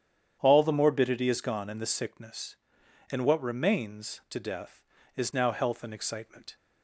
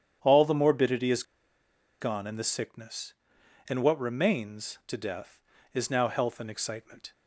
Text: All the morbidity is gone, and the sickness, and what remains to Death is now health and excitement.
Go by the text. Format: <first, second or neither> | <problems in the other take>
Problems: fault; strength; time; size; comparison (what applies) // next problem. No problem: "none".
first | starts louder than the rest; strong; until 1.2 s; 9 dB; strong in the first // pauses between "is" and "gone"; noticeable; at 1.2 s; 0.78 s long